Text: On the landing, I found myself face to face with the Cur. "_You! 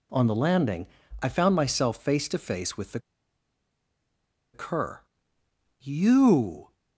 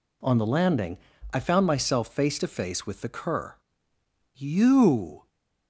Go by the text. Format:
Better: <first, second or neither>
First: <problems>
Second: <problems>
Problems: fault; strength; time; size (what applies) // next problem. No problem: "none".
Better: second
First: pauses between "the" and "Cur"; strong; at 2.9 s; 1.5 s long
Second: none